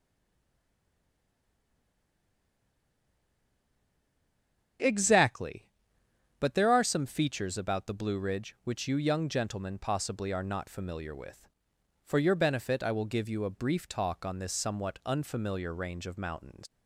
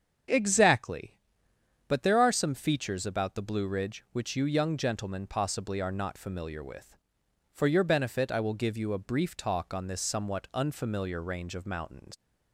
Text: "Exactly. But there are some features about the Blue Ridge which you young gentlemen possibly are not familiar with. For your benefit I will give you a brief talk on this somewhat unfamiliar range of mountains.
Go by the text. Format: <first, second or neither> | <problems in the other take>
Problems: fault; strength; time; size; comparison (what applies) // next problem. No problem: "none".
second | stays silent before the first word; strong; until 4.7 s; 4.7 s long // starts louder than the rest; strong; until 6.5 s; 7.5 dB; strong in the second